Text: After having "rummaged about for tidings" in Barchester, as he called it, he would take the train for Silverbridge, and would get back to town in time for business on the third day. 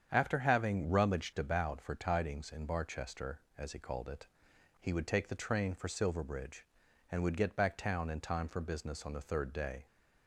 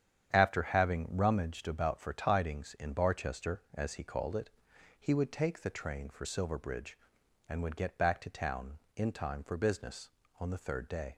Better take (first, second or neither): second